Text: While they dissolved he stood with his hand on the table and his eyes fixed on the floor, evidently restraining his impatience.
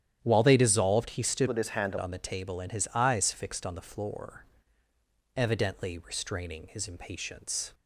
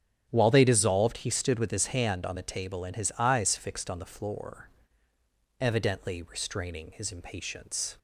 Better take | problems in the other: second | starts louder than the rest; strong; until 1.2 s; 10.5 dB; strong in the second // changes voice from "with" to "hand"; from 1.4 to 1.9 s; 0.5 s long

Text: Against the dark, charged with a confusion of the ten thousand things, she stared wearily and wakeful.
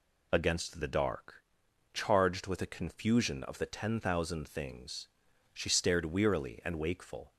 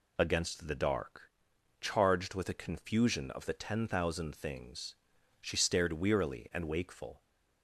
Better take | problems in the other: neither | none

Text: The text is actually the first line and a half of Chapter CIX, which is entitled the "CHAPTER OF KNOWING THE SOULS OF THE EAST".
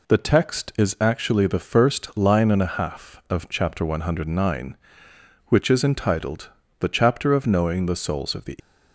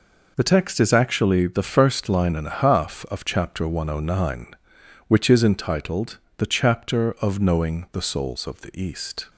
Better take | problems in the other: second | pauses between "entitled" and "the"; slight; at 6.5 s; 0.28 s long; slight in the second // stops before "EAST"; at 8.5 s

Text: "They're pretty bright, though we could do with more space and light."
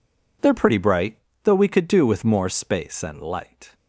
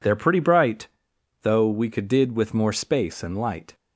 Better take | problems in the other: first | says "did" for "do"; at 2.0 s

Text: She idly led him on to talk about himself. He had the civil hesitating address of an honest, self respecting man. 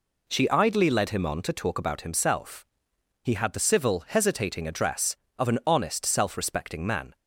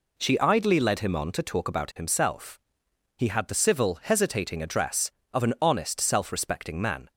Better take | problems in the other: neither | none

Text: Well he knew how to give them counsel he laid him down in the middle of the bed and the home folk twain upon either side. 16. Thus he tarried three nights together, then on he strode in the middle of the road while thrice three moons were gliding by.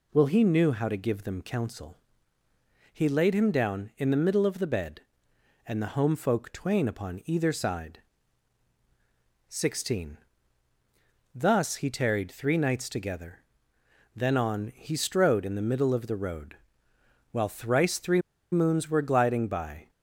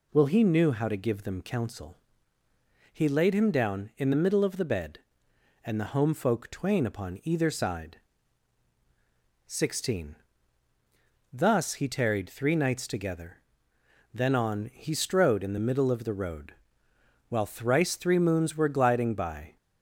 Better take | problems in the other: second | pauses between "counsel" and "he"; noticeable; at 1.9 s; 0.94 s long; noticeable in the second // pauses between "road" and "while"; noticeable; at 16.5 s; 0.76 s long; noticeable in the second // pauses between "three" and "moons"; slight; at 18.2 s; 0.30 s long

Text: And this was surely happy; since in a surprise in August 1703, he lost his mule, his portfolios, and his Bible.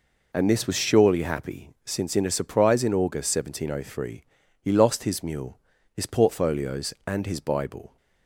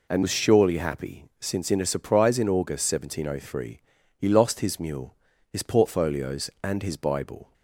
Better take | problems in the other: first | skips "this"; at 0.2 s

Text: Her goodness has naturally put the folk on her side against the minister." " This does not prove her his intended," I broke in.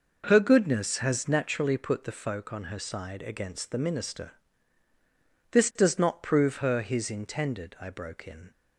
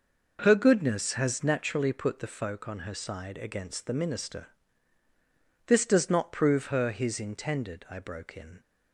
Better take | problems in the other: neither | starts louder than the rest; noticeable; the same in both

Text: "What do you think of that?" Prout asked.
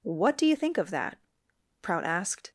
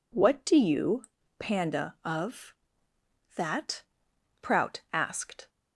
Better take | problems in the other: first | says "panda" for "think"; at 1.3 s

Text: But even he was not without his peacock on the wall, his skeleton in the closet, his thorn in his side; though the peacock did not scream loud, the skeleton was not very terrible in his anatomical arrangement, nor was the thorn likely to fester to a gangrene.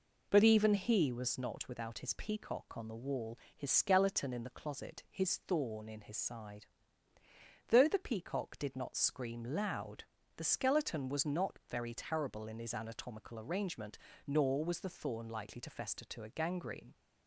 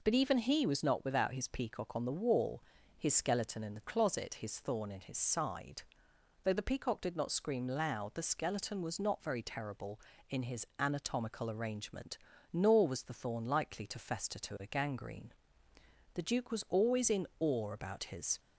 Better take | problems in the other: first | goes on to say "The Duke was always in awe about his"; strong; from 16.1 s on; 2.2 s long

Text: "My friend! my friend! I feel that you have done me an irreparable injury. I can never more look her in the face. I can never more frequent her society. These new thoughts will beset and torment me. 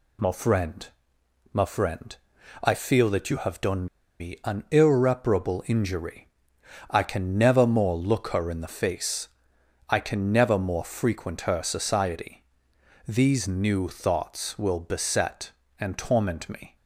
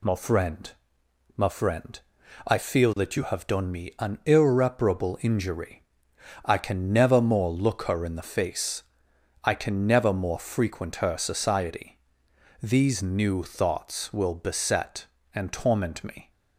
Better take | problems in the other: second | pauses between "done" and "me"; slight; at 3.8 s; 0.34 s long

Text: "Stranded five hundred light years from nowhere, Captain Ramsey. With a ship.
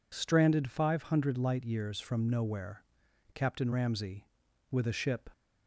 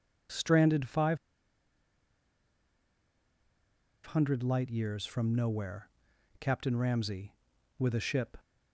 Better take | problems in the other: first | pauses between "five" and "hundred"; strong; at 1.1 s; 2.8 s long

